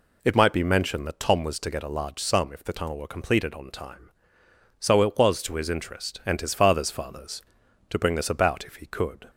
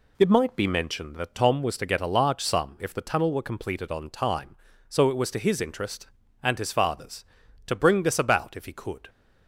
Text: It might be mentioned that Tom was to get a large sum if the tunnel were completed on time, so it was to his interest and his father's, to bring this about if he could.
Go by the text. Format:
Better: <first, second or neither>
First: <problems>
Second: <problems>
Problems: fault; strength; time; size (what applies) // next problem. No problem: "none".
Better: second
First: says "father's" twice; at 6.8 s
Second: none